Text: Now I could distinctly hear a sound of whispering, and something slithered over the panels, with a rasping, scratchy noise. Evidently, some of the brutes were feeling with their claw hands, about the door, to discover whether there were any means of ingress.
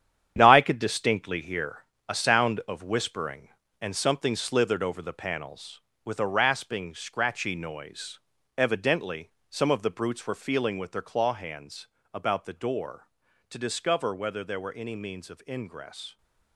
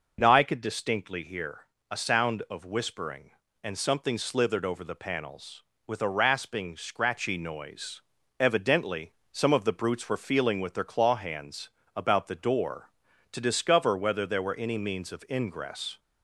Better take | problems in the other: second | gets quieter; strong; throughout; 9.5 dB // pauses between "hear" and "a"; slight; at 1.7 s; 0.28 s long; slight in the second

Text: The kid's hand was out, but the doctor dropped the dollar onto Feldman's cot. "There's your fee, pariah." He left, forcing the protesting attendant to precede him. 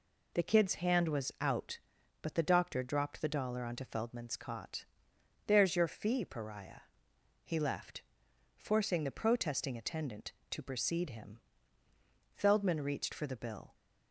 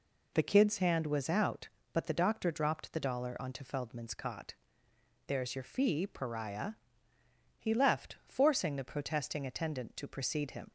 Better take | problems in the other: second | goes on to say "Feldman reached for the bill"; from 12.3 s on; 1.4 s long

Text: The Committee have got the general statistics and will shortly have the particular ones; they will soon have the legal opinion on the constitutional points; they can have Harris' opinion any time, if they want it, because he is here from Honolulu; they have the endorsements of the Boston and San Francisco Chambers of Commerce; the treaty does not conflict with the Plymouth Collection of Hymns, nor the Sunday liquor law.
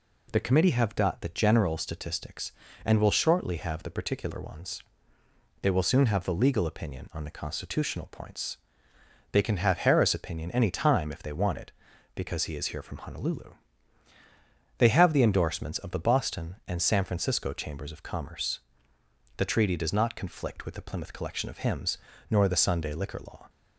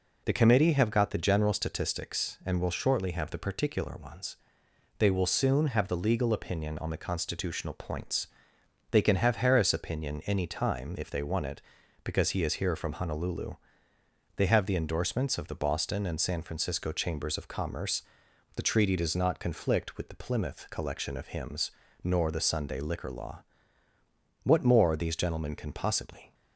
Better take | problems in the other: first | goes on to say "What more these gentlemen can possibly"; strong; from 24.4 s on; 1.9 s long

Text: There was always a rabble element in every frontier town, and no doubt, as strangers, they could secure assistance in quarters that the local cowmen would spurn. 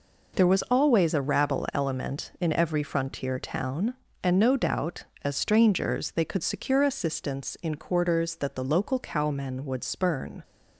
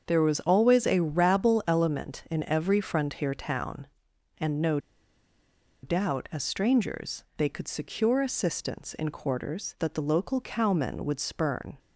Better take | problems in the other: first | starts louder than the rest; until 1.0 s; 7 dB // pauses between "no" and "doubt"; at 4.7 s; 1.0 s long

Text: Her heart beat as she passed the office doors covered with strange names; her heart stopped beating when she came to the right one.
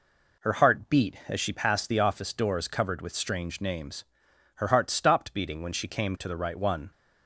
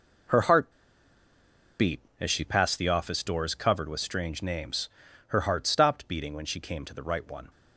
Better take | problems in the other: first | pauses between "heart" and "beat"; at 0.7 s; 1.0 s long

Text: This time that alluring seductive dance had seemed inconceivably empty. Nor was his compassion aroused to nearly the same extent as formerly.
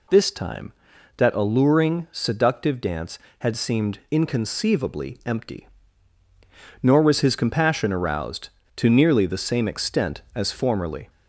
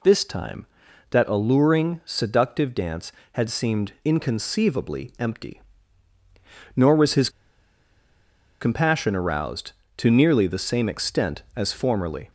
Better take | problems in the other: first | pauses between "his" and "compassion"; strong; at 7.3 s; 1.3 s long

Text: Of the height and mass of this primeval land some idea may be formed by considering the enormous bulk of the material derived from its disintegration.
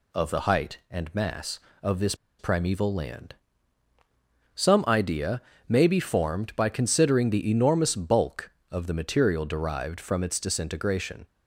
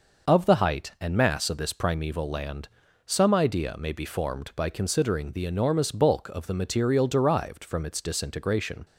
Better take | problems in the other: second | pauses between "this" and "primeval"; slight; at 2.1 s; 0.24 s long // pauses between "land" and "some"; at 3.3 s; 1.2 s long; also in the second // pauses between "idea" and "may"; slight; at 5.4 s; 0.28 s long

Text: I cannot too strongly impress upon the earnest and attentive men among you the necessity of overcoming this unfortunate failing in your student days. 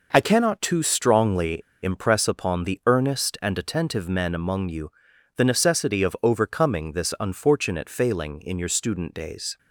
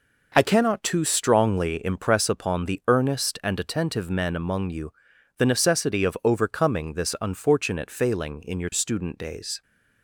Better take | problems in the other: second | pauses between "strongly" and "impress"; slight; at 1.6 s; 0.21 s long // pauses between "you" and "the"; noticeable; at 4.8 s; 0.46 s long; noticeable in the second

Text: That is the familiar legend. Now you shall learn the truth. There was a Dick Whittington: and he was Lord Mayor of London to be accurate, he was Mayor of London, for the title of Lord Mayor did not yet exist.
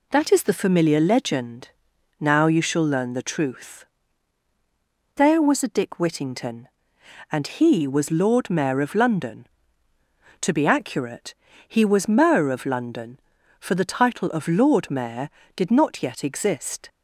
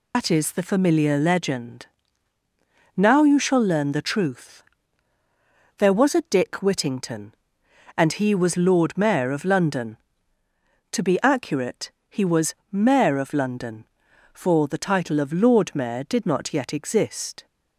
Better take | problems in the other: first | loses the start of "That"; at 0.1 s; 95 ms // pauses between "was" and "Mayor"; slight; at 12.5 s; 0.18 s long

